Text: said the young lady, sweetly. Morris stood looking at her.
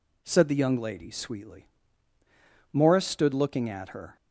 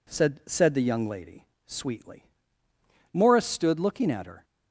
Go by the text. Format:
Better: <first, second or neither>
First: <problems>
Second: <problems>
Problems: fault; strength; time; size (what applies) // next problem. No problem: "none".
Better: first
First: none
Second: says "said" twice; at 0.4 s